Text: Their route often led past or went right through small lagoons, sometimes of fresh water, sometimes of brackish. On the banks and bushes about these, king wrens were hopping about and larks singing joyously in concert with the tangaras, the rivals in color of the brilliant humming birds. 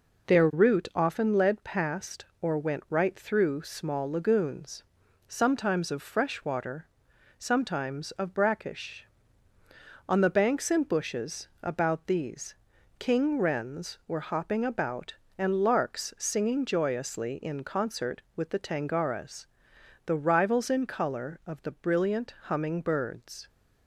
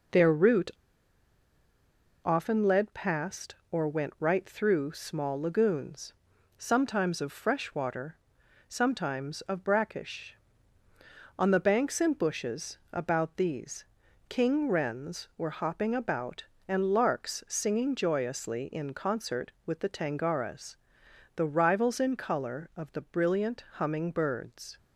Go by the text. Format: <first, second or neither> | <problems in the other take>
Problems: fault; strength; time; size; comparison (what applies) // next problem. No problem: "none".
first | pauses between "route" and "often"; strong; at 0.7 s; 1.5 s long